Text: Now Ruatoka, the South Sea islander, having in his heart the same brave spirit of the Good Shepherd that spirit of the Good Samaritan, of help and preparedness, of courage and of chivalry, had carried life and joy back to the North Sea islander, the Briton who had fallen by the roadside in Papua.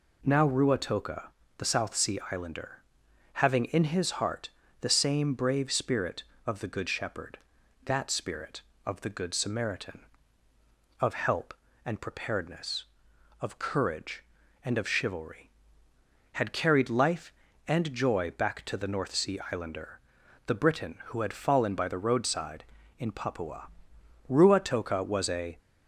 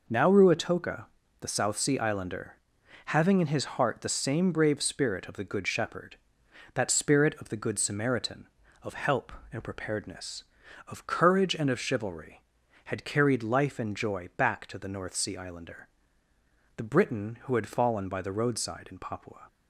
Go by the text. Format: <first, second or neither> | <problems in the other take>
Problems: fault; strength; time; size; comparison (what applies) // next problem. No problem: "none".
second | pauses between "heart" and "the"; slight; at 4.4 s; 0.30 s long // goes on to say "Ruatoka was a"; noticeable; from 24.2 s on; 1.3 s long